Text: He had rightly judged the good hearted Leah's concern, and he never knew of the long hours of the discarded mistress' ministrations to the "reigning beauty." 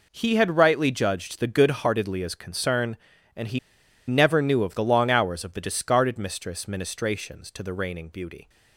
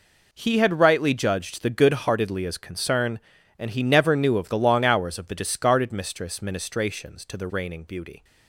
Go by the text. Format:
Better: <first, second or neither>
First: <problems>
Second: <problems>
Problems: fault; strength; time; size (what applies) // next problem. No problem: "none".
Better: second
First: pauses between "he" and "never"; noticeable; at 3.5 s; 0.49 s long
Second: none